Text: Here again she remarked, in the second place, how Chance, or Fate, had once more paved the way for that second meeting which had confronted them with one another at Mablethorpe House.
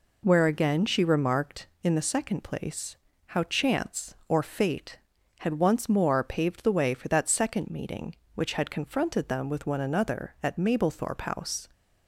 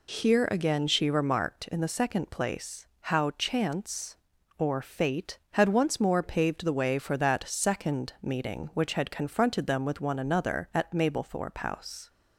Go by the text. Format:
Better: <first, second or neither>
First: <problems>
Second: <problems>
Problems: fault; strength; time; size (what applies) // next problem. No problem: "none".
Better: second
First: says "Where" for "Here"; at 0.2 s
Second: none